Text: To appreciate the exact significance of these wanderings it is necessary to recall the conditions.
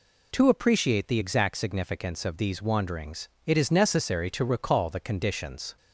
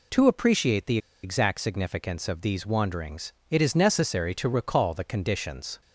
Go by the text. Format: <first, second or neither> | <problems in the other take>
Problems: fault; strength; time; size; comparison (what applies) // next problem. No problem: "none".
first | pauses between "the" and "exact"; slight; at 0.9 s; 0.25 s long // pauses between "wanderings" and "it"; slight; at 3.3 s; 0.16 s long; slight in the first